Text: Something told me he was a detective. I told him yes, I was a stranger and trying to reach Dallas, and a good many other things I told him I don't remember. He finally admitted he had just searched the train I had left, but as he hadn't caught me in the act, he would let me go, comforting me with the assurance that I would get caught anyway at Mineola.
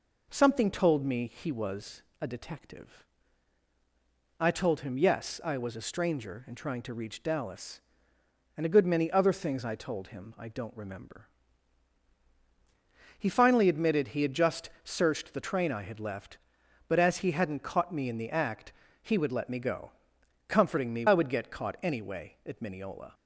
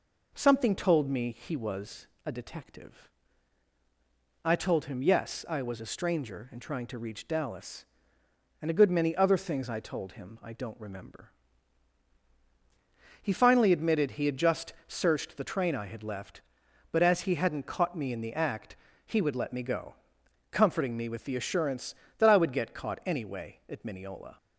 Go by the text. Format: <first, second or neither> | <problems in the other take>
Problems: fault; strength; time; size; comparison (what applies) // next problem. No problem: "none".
second | pauses between "was" and "a"; slight; at 2.0 s; 0.18 s long; slight in the second // skips "with the assurance that"; at 21.0 s